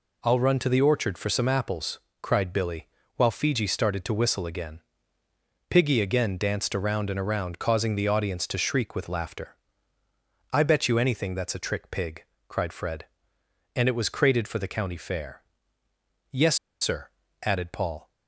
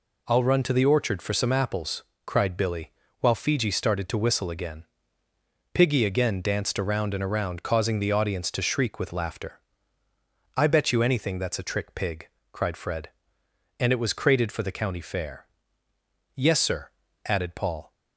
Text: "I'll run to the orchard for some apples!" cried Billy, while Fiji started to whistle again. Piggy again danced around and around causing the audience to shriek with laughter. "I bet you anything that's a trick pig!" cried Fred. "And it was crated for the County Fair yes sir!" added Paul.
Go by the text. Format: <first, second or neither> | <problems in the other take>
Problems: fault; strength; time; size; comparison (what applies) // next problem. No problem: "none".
second | pauses between "Fair" and "yes"; noticeable; at 15.4 s; 0.88 s long; noticeable in the second // pauses between "yes" and "sir"; slight; at 16.5 s; 0.25 s long